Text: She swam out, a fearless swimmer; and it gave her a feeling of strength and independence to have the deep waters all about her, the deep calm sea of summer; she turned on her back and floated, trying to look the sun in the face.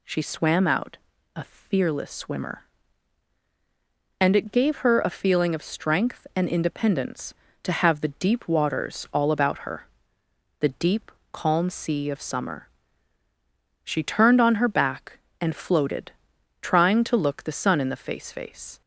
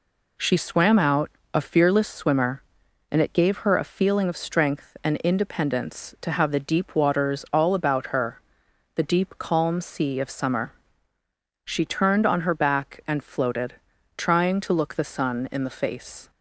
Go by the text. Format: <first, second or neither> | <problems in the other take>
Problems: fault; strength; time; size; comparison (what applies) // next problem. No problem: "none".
second | pauses between "deep" and "calm"; slight; at 11.1 s; 0.20 s long // says "face" twice; at 18.3 s